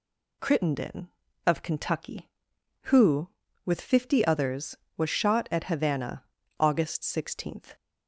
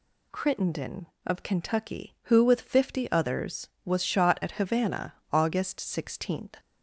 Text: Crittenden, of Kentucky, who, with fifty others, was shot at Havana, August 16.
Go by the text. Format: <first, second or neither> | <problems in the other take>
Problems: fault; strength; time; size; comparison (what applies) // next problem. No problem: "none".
neither | none